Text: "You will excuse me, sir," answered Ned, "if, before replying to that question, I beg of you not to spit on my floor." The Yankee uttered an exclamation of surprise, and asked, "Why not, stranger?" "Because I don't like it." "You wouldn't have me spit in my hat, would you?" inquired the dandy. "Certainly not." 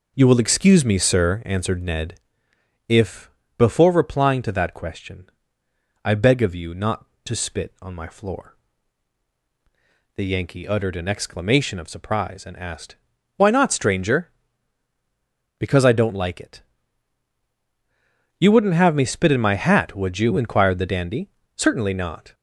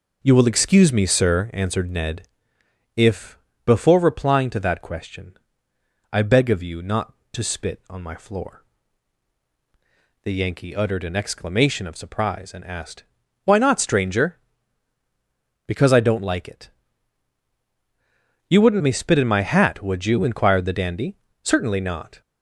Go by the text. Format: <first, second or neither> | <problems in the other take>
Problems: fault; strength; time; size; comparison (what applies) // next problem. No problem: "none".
first | skips "have"; at 18.8 s